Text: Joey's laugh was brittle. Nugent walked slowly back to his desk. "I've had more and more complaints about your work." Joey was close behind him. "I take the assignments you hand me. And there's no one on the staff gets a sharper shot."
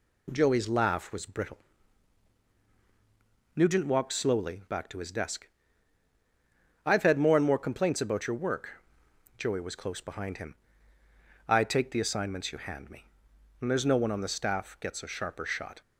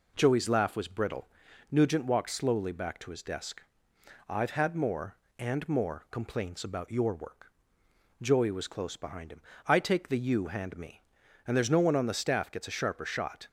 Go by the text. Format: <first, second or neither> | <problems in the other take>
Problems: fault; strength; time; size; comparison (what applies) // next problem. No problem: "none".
first | skips "assignments"; at 10.1 s